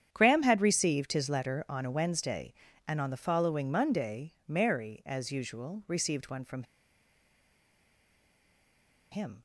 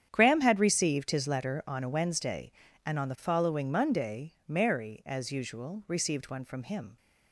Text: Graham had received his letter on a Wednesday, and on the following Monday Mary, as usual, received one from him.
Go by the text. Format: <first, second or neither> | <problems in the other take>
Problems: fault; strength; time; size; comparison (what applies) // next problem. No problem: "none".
second | starts louder than the rest; strong; until 1.1 s; 9 dB; strong in the second // pauses between "from" and "him"; strong; at 6.6 s; 2.4 s long